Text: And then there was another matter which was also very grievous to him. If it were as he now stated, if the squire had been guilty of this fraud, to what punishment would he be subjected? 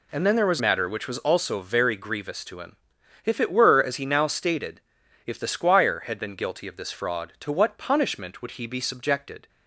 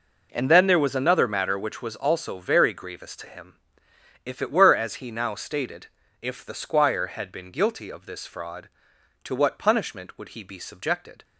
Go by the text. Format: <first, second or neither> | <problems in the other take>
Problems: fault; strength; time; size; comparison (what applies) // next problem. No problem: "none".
second | skips "another"; at 0.5 s